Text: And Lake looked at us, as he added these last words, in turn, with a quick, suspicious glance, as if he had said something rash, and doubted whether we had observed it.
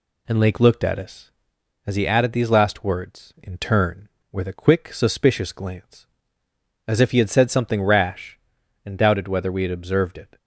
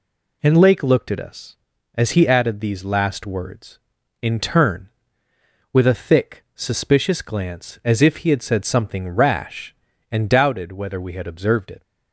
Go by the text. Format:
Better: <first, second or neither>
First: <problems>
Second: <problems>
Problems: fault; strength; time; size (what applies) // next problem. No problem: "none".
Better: first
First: none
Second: says "thick" for "quick"; at 5.9 s